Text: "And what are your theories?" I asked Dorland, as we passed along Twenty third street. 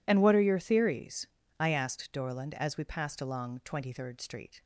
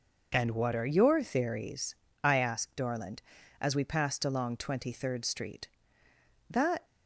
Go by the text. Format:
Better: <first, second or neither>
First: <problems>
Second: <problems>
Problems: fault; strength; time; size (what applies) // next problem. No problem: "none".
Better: first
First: none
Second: goes on to say "That"; slight; from 6.4 s on; 0.36 s long